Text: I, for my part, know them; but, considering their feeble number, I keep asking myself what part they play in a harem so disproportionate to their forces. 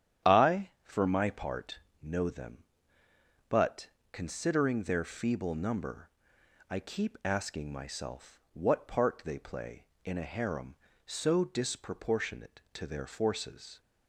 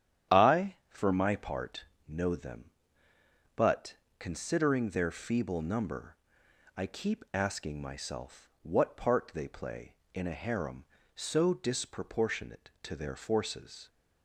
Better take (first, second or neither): neither